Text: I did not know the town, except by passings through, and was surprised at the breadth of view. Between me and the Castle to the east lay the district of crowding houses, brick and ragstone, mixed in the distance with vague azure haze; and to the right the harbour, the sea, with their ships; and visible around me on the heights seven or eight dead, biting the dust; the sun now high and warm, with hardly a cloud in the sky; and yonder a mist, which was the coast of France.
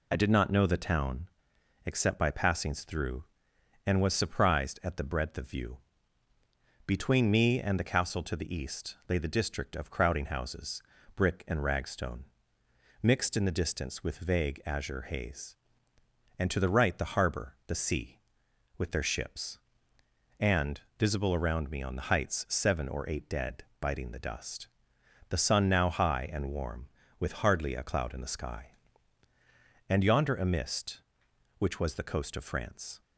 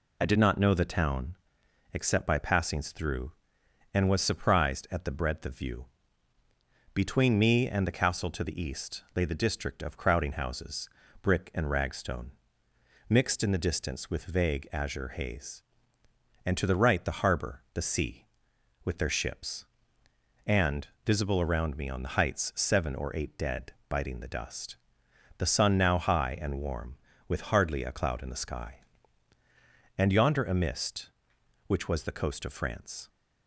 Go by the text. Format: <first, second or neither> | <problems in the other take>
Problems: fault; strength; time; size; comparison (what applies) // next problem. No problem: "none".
neither | pauses between "and" and "visible"; slight; the same in both